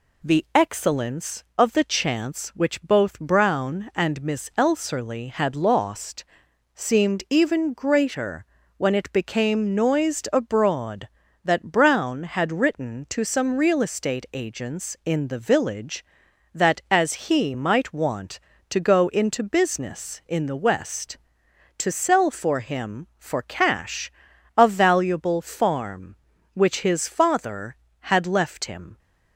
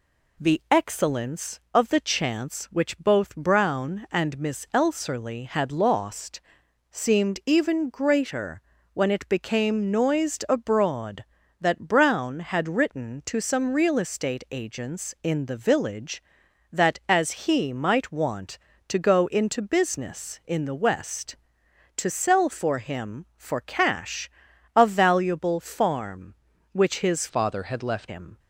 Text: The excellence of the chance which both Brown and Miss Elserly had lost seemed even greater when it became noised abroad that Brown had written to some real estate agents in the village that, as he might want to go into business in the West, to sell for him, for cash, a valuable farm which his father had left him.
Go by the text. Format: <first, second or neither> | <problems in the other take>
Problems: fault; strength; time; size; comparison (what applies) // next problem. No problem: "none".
first | pauses between "lost" and "seemed"; noticeable; at 6.3 s; 0.54 s long; noticeable in the first // pauses between "greater" and "when"; slight; at 8.6 s; 0.32 s long; slight in the first // changes voice from "father" to "left"; from 27.2 to 28.0 s; 0.8 s long